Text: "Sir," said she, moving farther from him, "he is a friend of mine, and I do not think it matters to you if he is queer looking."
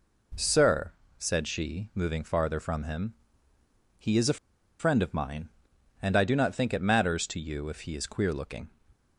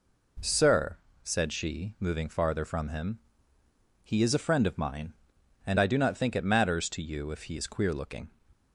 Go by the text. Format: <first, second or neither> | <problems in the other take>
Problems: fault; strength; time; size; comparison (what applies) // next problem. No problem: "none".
second | pauses between "a" and "friend"; at 4.3 s; 0.41 s long